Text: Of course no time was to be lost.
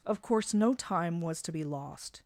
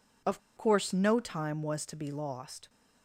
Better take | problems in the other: first | pauses between "Of" and "course"; slight; at 0.4 s; 0.17 s long

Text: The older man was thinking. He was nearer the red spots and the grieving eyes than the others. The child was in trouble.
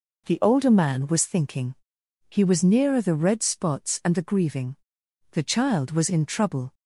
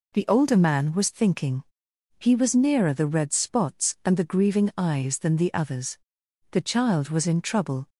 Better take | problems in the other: second | skips "eyes than the others"; at 5.0 s

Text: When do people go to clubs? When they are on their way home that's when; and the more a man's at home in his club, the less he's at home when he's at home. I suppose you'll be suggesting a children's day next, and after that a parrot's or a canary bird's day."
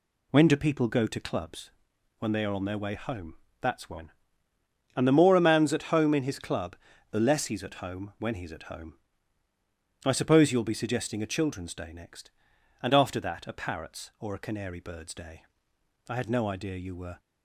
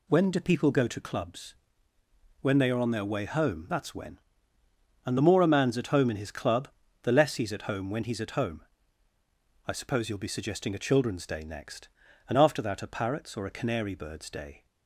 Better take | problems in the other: second | pauses between "home" and "that's"; slight; at 3.3 s; 0.26 s long // goes on to say "I had no idea you were"; noticeable; from 16.0 s on; 1.1 s long

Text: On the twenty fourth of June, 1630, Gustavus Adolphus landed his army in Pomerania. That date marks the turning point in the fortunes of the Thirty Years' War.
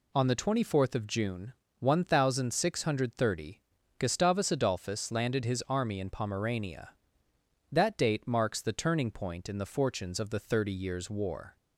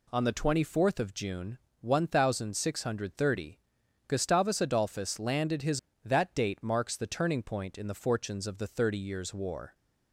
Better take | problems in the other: first | skips "army in Pomerania"; at 5.9 s

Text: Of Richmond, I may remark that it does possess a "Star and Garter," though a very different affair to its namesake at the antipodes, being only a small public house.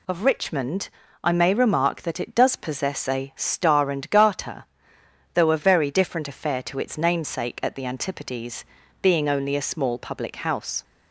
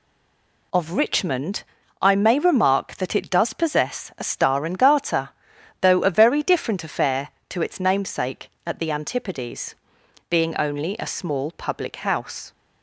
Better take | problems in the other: first | stays silent before the first word; slight; until 0.7 s; 0.7 s long

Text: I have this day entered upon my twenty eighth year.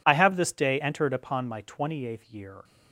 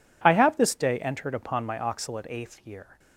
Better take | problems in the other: first | says "oxalate" for "twenty"; at 1.7 s

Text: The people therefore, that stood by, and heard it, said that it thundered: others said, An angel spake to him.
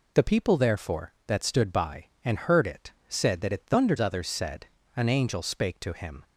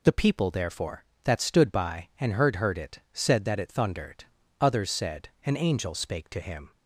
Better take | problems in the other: first | says "heard" twice; at 2.5 s

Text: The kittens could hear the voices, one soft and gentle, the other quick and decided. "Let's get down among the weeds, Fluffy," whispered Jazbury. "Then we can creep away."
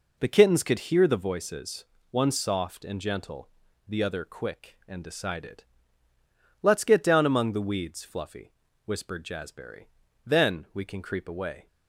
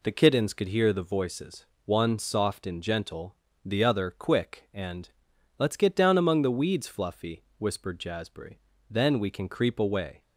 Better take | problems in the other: first | skips "decided"; at 5.3 s

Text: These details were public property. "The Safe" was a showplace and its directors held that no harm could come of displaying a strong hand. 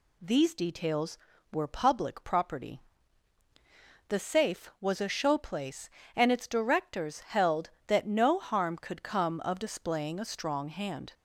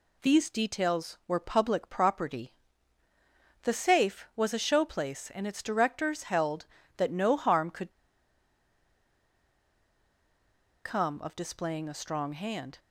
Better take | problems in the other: first | pauses between "could" and "come"; strong; at 7.9 s; 2.9 s long

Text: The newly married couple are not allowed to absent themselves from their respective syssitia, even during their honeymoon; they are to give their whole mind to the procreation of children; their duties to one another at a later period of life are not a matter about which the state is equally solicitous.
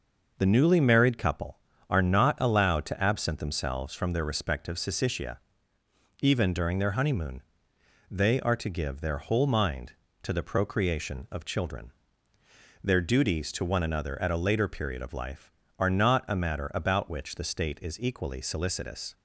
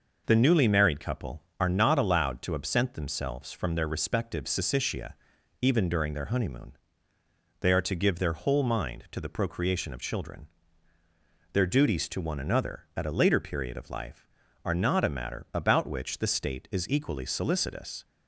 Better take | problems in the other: neither | none

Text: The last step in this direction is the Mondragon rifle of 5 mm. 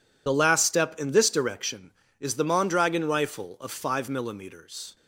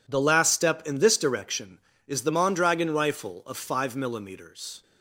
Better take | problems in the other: second | loses the start of "The"; at 0.2 s; 50 ms

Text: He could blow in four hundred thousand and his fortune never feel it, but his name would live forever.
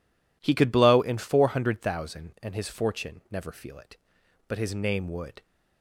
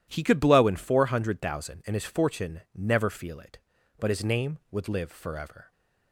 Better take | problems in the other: second | stops before "live forever"; at 5.4 s

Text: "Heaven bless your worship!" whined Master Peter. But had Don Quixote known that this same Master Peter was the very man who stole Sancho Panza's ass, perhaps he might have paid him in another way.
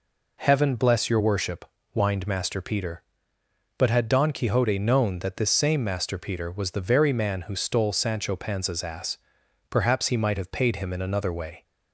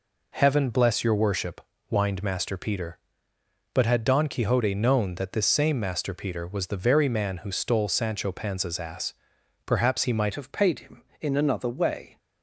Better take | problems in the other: first | changes voice at "have"; from 10.3 s on; 1.8 s long

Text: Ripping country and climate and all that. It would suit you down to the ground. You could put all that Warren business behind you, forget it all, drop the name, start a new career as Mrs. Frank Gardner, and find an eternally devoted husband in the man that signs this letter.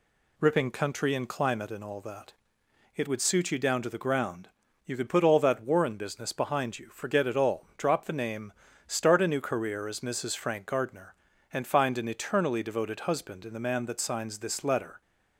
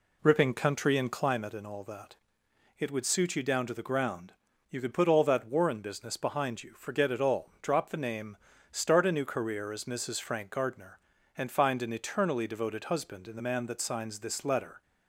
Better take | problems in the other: first | starts louder than the rest; slight; until 1.3 s; 2 dB

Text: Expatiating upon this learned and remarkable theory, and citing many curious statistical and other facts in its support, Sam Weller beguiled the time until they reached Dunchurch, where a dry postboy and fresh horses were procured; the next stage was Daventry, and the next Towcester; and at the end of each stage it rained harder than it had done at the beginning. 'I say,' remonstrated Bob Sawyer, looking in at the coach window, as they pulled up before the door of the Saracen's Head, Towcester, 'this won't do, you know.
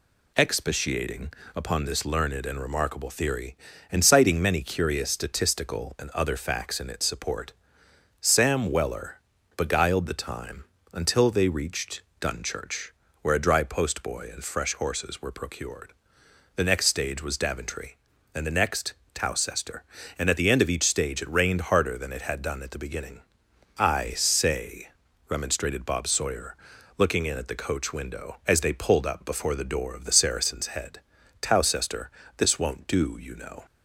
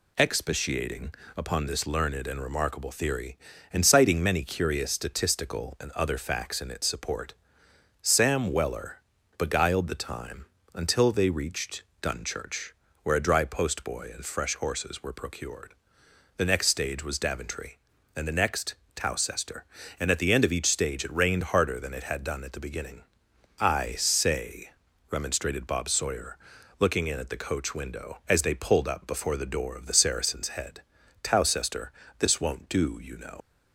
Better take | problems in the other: first | pauses between "Expatiating" and "upon"; slight; at 1.1 s; 0.24 s long; slight in the first // pauses between "Weller" and "beguiled"; at 8.9 s; 0.38 s long; also in the first // pauses between "time" and "until"; slight; at 10.4 s; 0.26 s long; slight in the first // pauses between "reached" and "Dunchurch"; slight; at 11.8 s; 0.18 s long; slight in the first // pauses between "next" and "Towcester"; slight; at 18.7 s; 0.18 s long; slight in the first // leaves "know" unfinished; at 33.4 s; 65 ms

